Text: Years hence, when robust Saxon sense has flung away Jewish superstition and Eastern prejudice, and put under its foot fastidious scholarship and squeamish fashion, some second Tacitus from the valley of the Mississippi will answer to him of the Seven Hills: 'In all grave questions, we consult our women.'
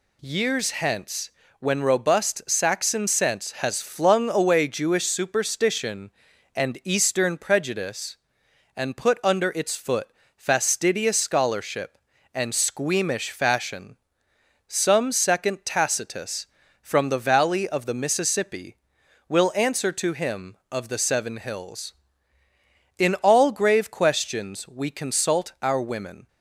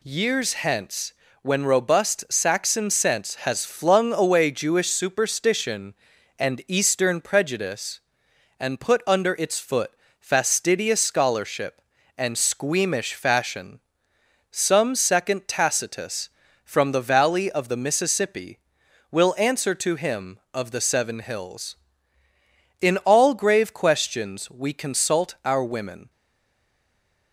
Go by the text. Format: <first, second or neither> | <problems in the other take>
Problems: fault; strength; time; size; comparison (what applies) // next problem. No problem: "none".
first | pauses between "foot" and "fastidious"; slight; at 9.9 s; 0.28 s long; slight in the first // stays silent after the last word; noticeable; from 26.0 s on; 1.3 s long